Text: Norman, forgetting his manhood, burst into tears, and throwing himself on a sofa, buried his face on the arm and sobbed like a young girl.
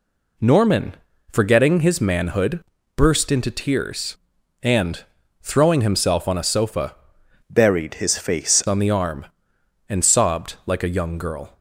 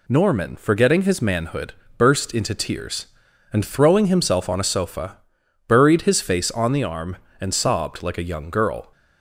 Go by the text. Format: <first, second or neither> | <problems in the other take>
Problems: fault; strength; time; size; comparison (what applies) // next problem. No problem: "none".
second | pauses between "and" and "throwing"; at 5.0 s; 0.38 s long // changes voice from "buried" to "face"; from 7.4 to 8.6 s; 1.2 s long